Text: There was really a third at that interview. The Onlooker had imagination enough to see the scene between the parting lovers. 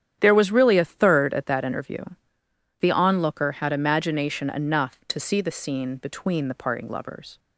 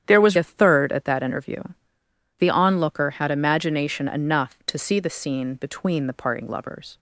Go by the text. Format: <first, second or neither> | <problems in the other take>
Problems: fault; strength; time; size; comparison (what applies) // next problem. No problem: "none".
first | starts louder than the rest; strong; until 1.0 s; 9.5 dB; strong in the first // skips "really"; at 0.3 s